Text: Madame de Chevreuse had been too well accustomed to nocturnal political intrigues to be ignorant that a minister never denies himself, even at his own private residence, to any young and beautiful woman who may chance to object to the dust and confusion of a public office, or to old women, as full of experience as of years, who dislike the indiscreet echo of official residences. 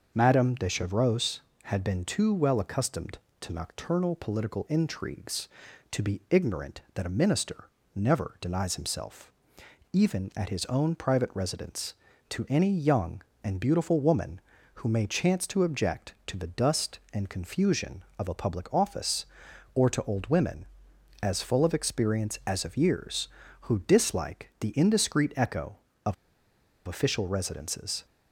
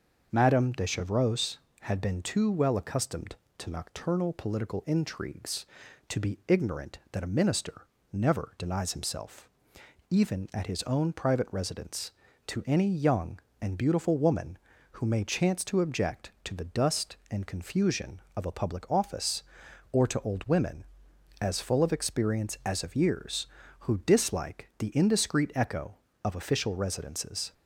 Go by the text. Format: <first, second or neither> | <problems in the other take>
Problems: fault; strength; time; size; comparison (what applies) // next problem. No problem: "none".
second | starts louder than the rest; until 1.1 s; 6 dB; also in the second // pauses between "minister" and "never"; slight; at 7.6 s; 0.26 s long; slight in the second // pauses between "of" and "official"; noticeable; at 26.1 s; 0.72 s long